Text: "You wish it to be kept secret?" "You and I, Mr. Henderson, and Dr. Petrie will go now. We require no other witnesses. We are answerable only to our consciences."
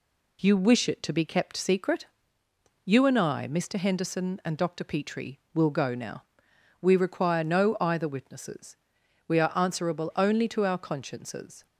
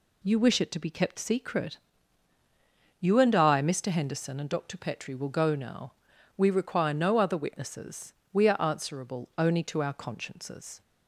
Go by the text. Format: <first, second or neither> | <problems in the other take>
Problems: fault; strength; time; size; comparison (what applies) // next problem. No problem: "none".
second | says "either" for "other"; at 7.7 s